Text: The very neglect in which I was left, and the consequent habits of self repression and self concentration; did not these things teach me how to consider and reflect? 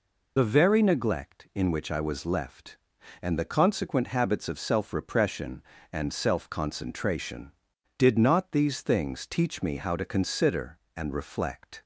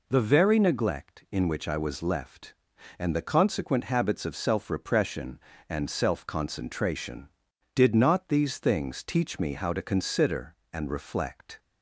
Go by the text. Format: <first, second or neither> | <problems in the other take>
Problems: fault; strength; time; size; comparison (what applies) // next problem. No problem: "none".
second | loses the start of "The"; at 0.3 s; 45 ms